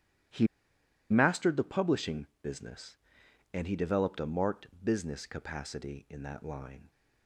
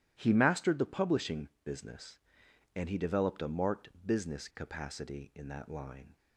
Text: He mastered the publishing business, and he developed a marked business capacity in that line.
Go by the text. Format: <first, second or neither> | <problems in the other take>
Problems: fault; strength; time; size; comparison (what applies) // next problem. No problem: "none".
second | starts louder than the rest; strong; until 1.9 s; 12 dB; strong in the second // pauses between "He" and "mastered"; noticeable; at 0.4 s; 0.63 s long // pauses between "marked" and "business"; slight; at 4.6 s; 0.16 s long; slight in the second